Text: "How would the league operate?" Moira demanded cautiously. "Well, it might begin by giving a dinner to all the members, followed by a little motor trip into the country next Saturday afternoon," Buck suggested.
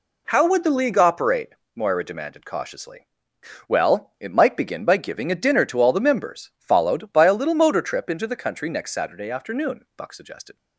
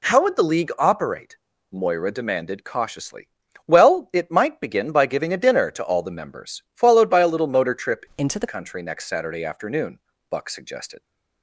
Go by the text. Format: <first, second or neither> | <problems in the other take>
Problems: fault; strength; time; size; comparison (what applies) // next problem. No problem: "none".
first | changes voice from "into" to "the"; from 8.1 to 8.4 s; 0.3 s long